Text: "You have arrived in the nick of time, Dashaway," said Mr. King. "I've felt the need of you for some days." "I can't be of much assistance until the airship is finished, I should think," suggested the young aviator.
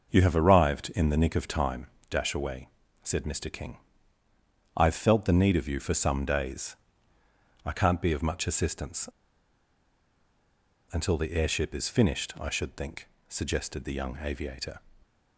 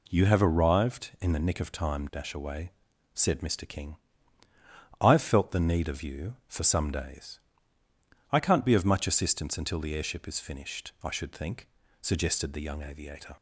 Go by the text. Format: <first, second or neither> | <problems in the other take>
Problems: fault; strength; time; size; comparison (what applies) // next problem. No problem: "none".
second | pauses between "assistance" and "until"; strong; at 9.0 s; 1.8 s long